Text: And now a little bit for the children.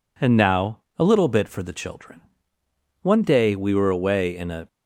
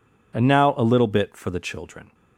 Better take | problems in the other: second | pauses between "now" and "a"; slight; at 0.7 s; 0.18 s long // goes on to say "One day we were away in a"; from 3.0 s on; 1.6 s long

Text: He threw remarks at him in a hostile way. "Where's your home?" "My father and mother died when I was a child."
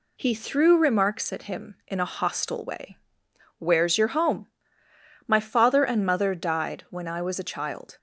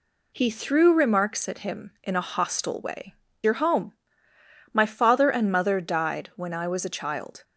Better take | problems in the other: first | skips "Where's"; at 3.2 s

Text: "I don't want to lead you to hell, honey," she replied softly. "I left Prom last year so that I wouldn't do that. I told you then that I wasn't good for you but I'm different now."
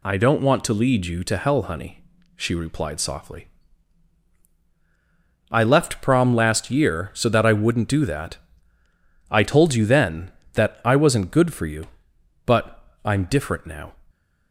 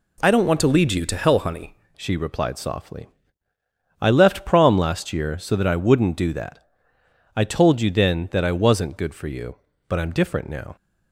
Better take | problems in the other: first | changes voice at "she"; from 1.9 s on; 8.8 s long

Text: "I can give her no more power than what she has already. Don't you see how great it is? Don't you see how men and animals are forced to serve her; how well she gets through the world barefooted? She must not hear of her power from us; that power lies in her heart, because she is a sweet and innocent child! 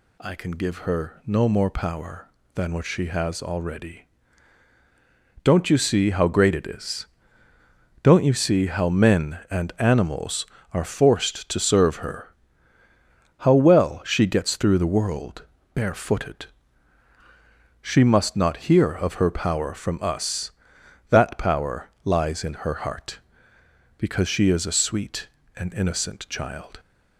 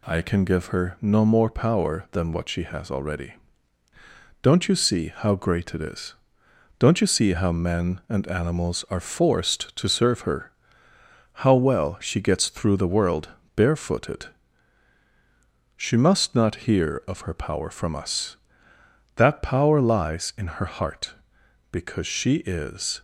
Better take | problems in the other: first | pauses between "world" and "barefooted"; slight; at 13.2 s; 0.26 s long; slight in the first // stops before "a sweet and innocent child"; at 22.9 s

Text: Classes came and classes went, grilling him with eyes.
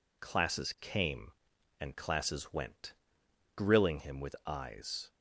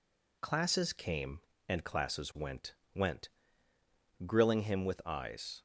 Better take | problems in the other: first | says "went" twice; at 2.9 s

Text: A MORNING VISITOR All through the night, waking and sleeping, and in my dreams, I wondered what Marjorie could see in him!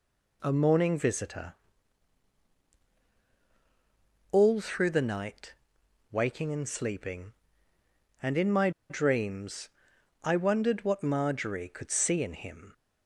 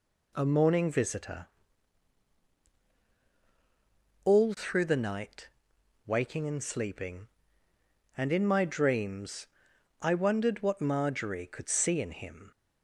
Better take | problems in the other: second | pauses between "VISITOR" and "All"; strong; at 1.5 s; 2.8 s long; strong in the second // pauses between "my" and "dreams"; slight; at 8.6 s; 0.19 s long

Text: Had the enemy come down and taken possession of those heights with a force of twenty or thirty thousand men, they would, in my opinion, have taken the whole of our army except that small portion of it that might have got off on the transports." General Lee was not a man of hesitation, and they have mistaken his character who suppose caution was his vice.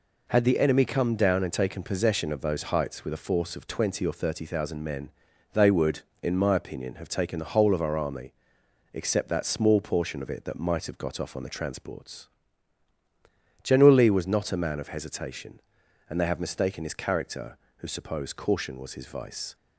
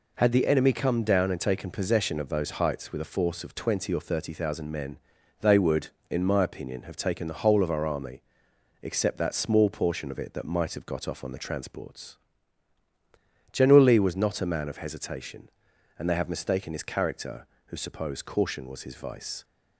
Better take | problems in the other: neither | pauses between "army" and "except"; noticeable; the same in both

